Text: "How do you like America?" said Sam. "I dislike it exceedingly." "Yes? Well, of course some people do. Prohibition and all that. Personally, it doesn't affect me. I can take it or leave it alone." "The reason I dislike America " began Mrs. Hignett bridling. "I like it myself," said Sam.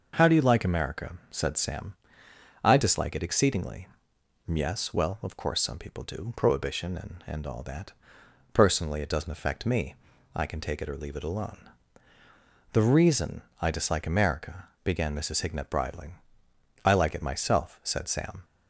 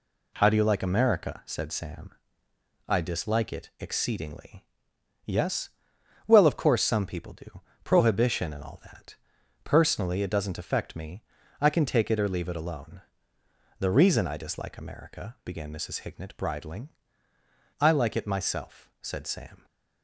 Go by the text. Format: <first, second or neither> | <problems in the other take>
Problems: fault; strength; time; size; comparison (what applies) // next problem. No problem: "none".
second | says "and" twice; at 7.2 s // pauses between "reason" and "I"; slight; at 13.4 s; 0.18 s long